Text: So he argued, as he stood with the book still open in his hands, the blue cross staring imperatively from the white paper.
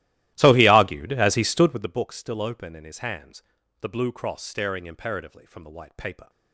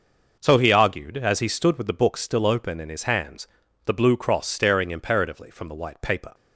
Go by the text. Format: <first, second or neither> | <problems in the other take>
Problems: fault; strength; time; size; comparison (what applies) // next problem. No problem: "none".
second | starts louder than the rest; strong; until 2.0 s; 15.5 dB